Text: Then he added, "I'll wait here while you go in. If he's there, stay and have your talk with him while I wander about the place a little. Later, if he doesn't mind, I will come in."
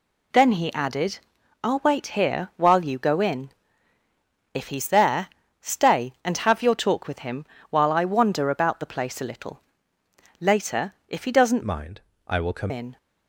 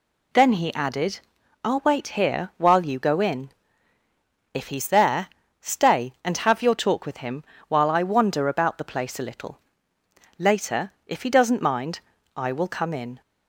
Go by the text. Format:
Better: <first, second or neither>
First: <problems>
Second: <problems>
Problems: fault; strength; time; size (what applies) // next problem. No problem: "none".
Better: second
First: pauses between "him" and "while"; slight; at 7.4 s; 0.24 s long // changes voice from "mind" to "come"; from 11.6 to 12.7 s; 1.1 s long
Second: pauses between "him" and "while"; slight; at 7.4 s; 0.24 s long